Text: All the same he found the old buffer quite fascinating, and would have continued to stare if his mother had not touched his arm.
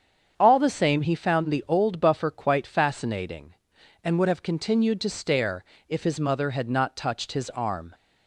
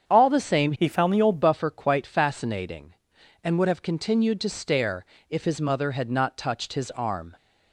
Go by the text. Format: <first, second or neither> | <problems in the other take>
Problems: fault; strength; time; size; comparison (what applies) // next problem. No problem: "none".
first | starts louder than the rest; strong; until 1.0 s; 7.5 dB; strong in the first // changes voice from "he" to "old"; from 0.7 to 1.3 s; 0.6 s long // pauses between "stare" and "if"; slight; at 5.0 s; 0.28 s long; slight in the first